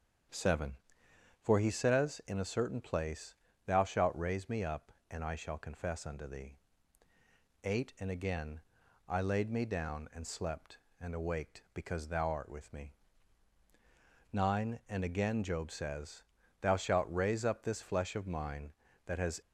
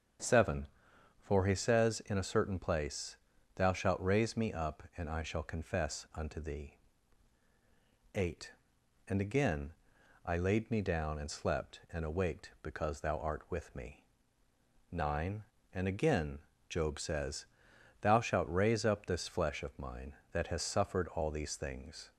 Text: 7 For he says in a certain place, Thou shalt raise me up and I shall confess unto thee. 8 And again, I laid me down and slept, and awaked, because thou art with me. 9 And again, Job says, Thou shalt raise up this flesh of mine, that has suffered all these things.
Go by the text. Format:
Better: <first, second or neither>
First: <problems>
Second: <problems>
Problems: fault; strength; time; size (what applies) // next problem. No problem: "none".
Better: second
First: starts louder than the rest; strong; until 1.9 s; 7.5 dB // stops before "suffered all these things"; at 19.4 s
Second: starts louder than the rest; strong; until 1.7 s; 7.5 dB